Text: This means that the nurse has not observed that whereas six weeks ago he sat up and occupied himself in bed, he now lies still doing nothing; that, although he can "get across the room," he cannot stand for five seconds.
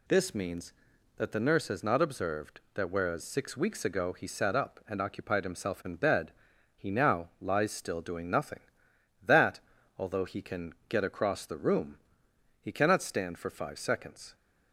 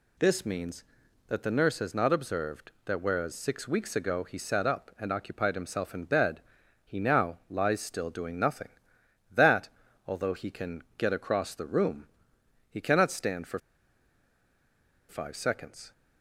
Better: first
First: pauses between "can" and "get"; slight; at 10.7 s; 0.16 s long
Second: pauses between "can" and "get"; slight; at 10.8 s; 0.16 s long // pauses between "for" and "five"; strong; at 13.5 s; 1.4 s long

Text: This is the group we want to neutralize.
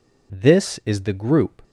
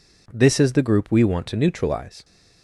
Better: second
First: stops before "we want to neutralize"; at 1.6 s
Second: none

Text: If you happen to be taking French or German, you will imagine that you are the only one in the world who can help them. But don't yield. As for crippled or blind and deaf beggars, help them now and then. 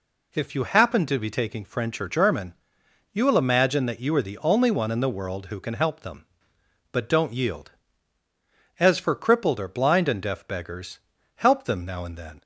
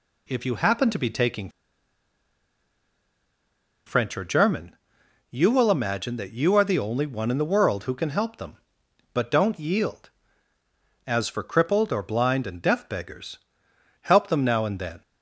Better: first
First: none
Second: pauses between "taking" and "French"; strong; at 1.4 s; 2.3 s long

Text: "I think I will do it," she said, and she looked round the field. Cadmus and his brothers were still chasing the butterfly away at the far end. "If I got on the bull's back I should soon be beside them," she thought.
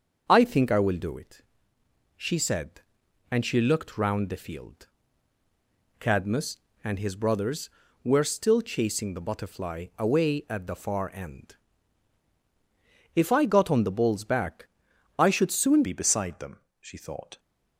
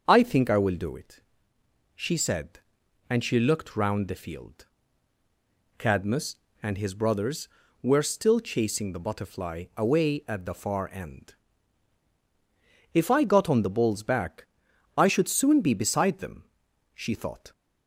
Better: second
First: starts louder than the rest; until 1.2 s; 6.5 dB // pauses between "back" and "I"; noticeable; at 14.6 s; 0.50 s long // changes voice at "be"; from 15.8 s on; 1.5 s long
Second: starts louder than the rest; until 1.0 s; 6.5 dB // pauses between "back" and "I"; noticeable; at 14.4 s; 0.50 s long

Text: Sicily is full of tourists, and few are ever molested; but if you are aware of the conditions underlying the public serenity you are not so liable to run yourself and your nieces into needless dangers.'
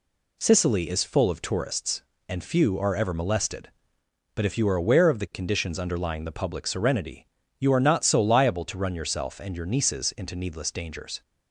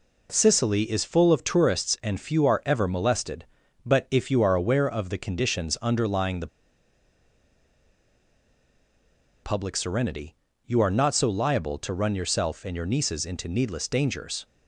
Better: first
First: pauses between "serenity" and "you"; slight; at 7.2 s; 0.32 s long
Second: pauses between "the" and "public"; strong; at 6.4 s; 2.9 s long // pauses between "serenity" and "you"; slight; at 10.3 s; 0.32 s long

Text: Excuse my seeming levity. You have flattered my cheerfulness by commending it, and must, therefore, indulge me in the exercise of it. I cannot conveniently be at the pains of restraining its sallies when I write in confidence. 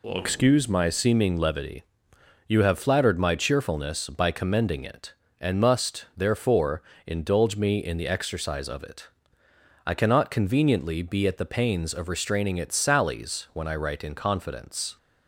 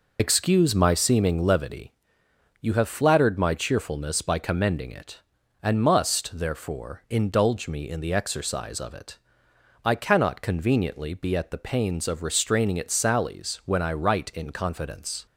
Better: first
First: none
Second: loses the start of "Excuse"; at 0.1 s; 50 ms

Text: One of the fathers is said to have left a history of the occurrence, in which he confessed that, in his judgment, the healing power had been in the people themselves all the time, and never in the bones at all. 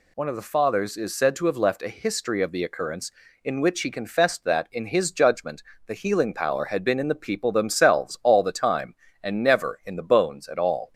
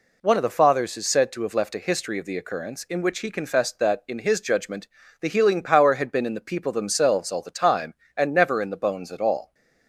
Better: neither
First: none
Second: none

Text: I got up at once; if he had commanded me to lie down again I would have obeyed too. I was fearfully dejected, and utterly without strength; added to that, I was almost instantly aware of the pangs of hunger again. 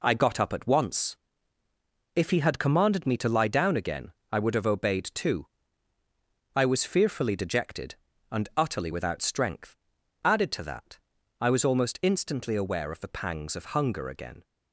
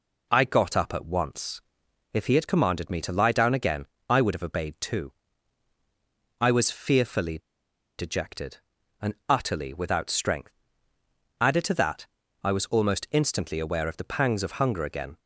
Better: first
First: pauses between "again" and "I"; slight; at 4.1 s; 0.22 s long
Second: pauses between "again" and "I"; slight; at 3.8 s; 0.22 s long // pauses between "fearfully" and "dejected"; noticeable; at 7.3 s; 0.58 s long

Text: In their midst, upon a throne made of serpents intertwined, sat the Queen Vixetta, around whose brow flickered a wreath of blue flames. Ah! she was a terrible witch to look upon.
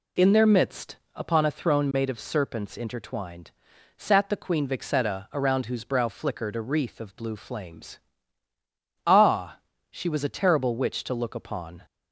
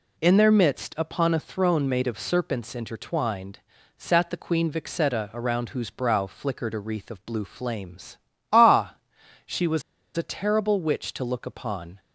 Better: first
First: none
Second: pauses between "was" and "a"; slight; at 9.8 s; 0.35 s long

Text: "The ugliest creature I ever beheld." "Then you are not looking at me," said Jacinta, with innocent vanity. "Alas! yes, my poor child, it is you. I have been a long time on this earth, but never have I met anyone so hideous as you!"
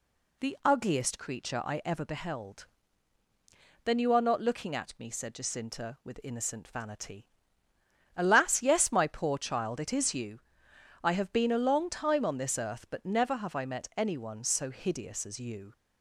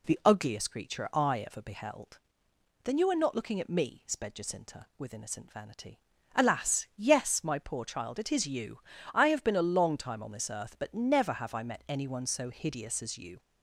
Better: first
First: none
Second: says "sped" for "said"; at 4.0 s

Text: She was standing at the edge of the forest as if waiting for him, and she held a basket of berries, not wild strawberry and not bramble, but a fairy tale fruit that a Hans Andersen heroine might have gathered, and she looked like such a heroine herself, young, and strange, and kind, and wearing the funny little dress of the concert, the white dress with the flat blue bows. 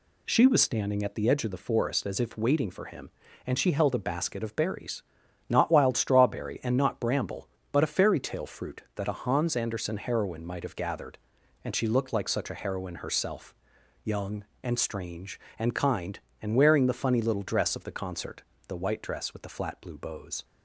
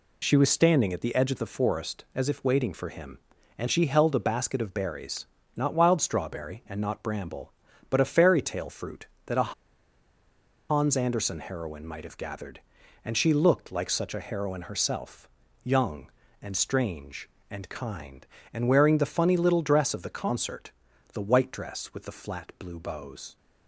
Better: first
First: none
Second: pauses between "a" and "Hans"; at 9.5 s; 1.1 s long

